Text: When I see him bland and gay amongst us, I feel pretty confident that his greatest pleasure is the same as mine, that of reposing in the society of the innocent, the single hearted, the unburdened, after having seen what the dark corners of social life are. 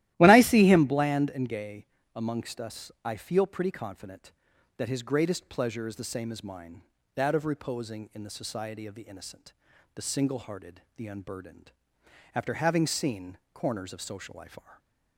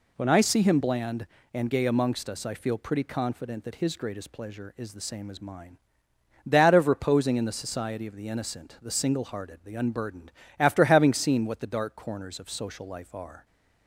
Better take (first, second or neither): second